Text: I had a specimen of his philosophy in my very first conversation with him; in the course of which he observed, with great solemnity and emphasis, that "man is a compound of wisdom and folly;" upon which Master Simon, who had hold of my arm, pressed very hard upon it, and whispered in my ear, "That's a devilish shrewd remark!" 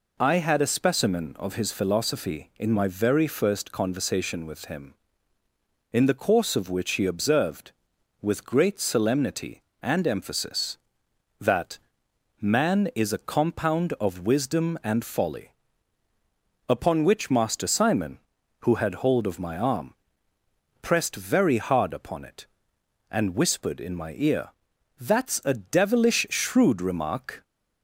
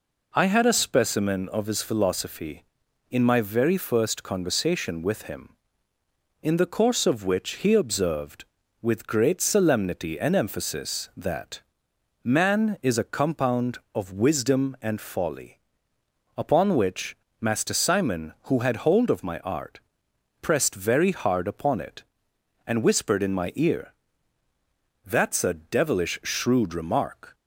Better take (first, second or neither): first